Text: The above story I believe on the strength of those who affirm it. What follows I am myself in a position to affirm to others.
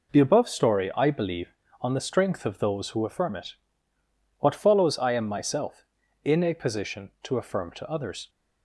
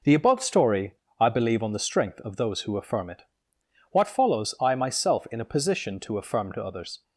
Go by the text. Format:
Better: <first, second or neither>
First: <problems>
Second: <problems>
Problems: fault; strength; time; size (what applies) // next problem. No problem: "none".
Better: first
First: none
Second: pauses between "story" and "I"; slight; at 0.9 s; 0.22 s long // skips "am"; at 4.7 s